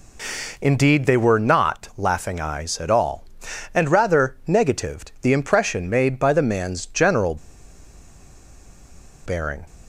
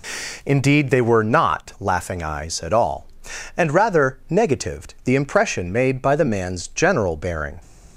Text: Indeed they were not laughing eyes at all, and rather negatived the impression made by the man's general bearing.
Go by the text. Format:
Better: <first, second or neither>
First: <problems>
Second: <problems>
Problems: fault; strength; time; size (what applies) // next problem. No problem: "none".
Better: second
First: pauses between "general" and "bearing"; strong; at 7.3 s; 1.8 s long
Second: none